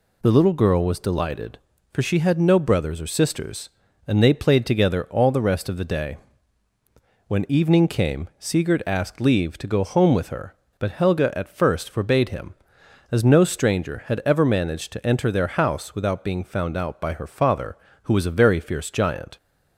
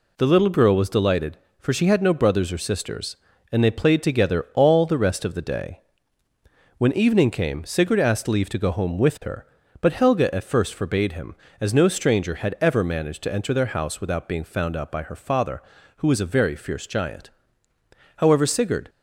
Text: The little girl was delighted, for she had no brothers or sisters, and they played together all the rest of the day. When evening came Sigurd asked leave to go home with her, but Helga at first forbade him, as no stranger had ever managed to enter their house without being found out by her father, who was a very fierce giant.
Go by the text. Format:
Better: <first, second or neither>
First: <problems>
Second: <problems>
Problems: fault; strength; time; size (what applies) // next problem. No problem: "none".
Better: first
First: none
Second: goes on to say "However Sigurd"; noticeable; from 18.1 s on; 0.72 s long